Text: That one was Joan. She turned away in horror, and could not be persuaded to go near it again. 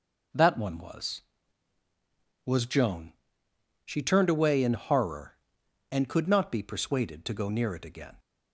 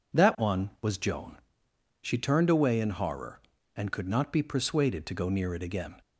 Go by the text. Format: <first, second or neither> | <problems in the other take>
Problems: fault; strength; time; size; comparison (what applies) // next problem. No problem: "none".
second | says "was" twice; at 2.4 s